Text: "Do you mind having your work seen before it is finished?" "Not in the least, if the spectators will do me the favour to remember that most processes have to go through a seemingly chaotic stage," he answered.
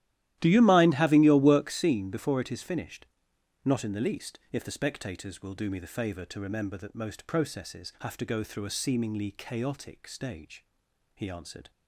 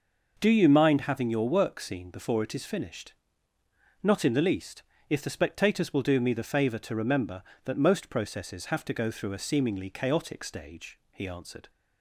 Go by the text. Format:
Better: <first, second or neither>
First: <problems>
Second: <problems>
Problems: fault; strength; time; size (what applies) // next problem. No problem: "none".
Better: second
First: starts louder than the rest; strong; until 1.8 s; 13.5 dB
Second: none